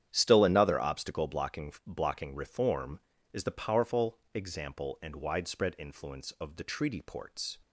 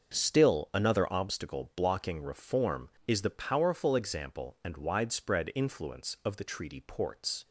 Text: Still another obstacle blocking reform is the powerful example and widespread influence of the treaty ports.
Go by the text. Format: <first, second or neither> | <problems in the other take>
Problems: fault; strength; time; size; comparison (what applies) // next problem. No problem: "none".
second | starts louder than the rest; strong; until 1.1 s; 9.5 dB; also in the second // says "blocking" twice; at 1.8 s // pauses between "powerful" and "example"; slight; at 4.1 s; 0.16 s long